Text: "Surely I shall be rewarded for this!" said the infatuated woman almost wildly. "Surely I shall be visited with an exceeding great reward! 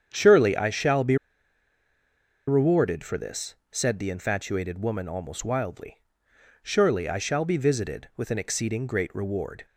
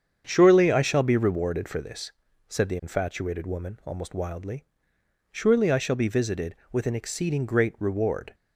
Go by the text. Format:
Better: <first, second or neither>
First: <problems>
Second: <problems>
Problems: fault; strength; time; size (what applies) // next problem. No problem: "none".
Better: second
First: starts louder than the rest; strong; until 1.1 s; 8 dB // pauses between "be" and "rewarded"; strong; at 1.1 s; 1.3 s long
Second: starts louder than the rest; strong; until 1.2 s; 7.5 dB